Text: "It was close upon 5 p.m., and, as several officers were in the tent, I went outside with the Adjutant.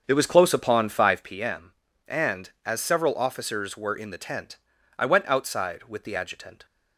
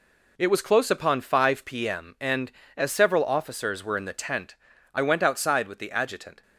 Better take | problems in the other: second | starts louder than the rest; until 1.4 s; 7 dB

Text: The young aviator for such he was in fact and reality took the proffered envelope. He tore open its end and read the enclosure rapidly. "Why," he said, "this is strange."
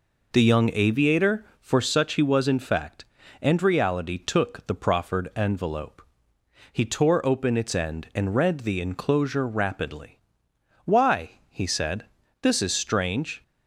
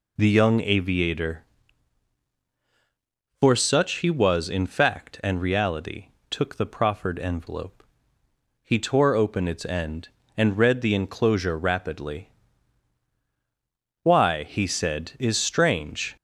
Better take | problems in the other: first | pauses between "reality" and "took"; slight; at 6.0 s; 0.24 s long // skips "this"; at 15.1 s

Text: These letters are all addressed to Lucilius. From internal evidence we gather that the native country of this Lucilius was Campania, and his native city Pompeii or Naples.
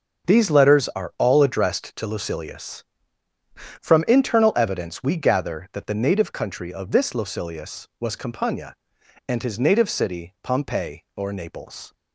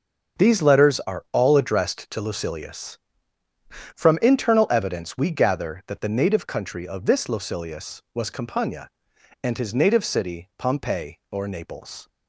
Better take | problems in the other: neither | starts louder than the rest; the same in both

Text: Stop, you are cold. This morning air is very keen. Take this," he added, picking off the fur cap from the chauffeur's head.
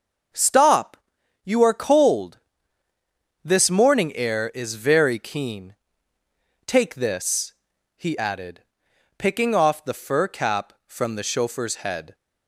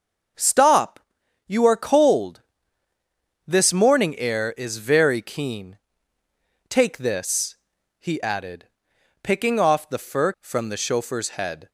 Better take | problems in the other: first | starts louder than the rest; until 1.8 s; 6.5 dB; also in the first // skips "cap"; at 10.3 s

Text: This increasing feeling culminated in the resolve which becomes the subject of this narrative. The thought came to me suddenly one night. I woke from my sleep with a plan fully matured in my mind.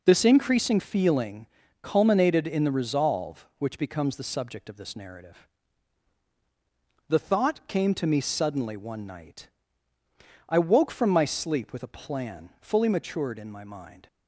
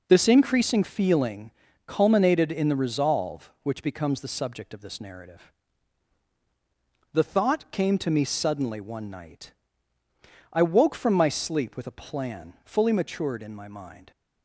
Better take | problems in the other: neither | pauses between "feeling" and "culminated"; the same in both

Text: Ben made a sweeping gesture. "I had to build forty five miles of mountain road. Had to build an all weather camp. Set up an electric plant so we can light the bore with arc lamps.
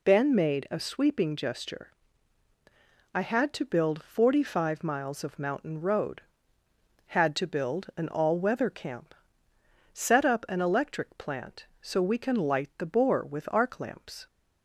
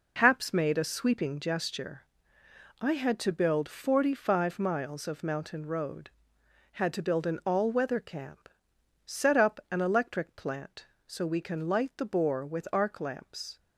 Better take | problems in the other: first | says "Haps" for "Ben"; at 0.1 s

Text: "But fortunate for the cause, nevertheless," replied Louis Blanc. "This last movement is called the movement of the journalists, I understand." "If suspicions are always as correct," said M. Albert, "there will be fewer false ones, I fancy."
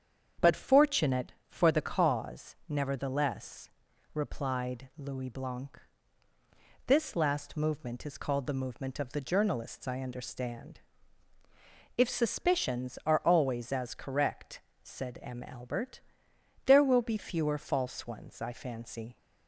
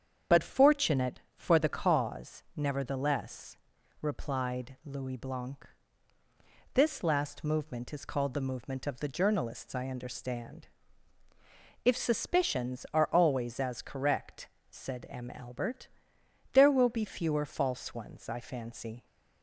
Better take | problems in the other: first | loses the start of "But"; at 0.3 s; 50 ms // starts louder than the rest; strong; until 1.4 s; 7.5 dB; strong in the first

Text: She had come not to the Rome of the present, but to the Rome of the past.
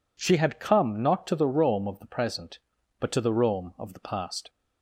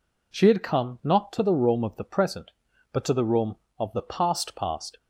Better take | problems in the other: first | says "past" twice; at 4.5 s

